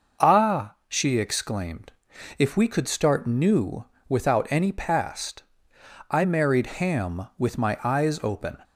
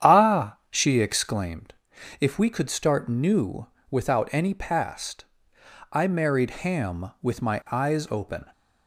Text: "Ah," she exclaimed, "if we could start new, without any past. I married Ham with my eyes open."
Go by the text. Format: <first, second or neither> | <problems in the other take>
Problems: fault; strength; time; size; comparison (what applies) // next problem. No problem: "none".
first | starts louder than the rest; strong; until 1.6 s; 9 dB // pauses between "married" and "Ham"; slight; at 6.5 s; 0.16 s long; slight in the first